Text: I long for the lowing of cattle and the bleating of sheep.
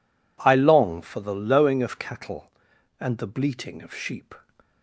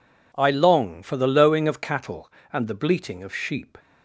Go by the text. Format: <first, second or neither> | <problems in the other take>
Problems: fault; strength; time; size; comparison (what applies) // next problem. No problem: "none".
neither | none